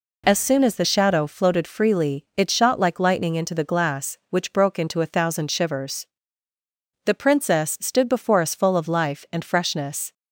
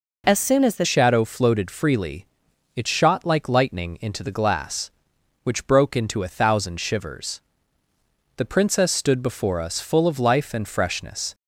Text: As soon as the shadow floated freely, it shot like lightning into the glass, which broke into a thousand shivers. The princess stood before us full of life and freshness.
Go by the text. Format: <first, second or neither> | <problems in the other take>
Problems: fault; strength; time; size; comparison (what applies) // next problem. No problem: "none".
first | changes voice at "shadow"; from 0.8 s on; 10.5 s long